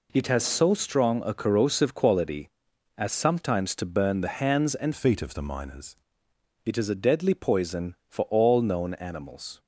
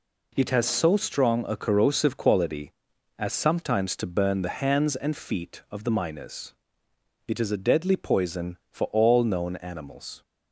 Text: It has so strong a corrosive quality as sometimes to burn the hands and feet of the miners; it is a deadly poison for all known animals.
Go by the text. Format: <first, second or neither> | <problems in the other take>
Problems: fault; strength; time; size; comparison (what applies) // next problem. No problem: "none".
second | changes voice from "feet" to "miners"; from 4.9 to 5.9 s; 1.0 s long